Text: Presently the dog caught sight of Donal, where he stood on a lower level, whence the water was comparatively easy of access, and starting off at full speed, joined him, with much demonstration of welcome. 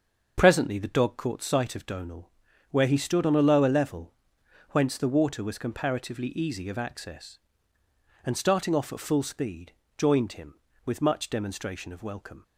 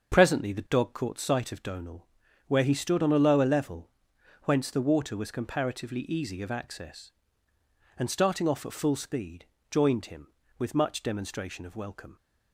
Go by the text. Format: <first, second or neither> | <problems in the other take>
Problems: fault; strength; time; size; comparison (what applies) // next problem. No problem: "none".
neither | starts louder than the rest; the same in both